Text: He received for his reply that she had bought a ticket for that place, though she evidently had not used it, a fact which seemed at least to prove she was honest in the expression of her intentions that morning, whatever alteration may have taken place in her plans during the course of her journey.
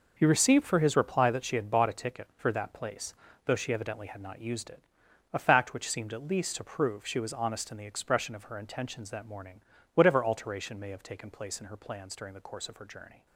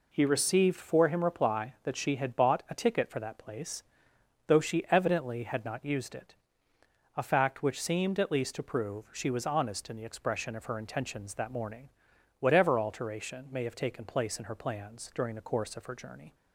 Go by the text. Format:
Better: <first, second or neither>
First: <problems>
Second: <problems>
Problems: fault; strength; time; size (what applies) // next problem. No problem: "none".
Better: first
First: none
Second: says "him" for "his"; at 1.0 s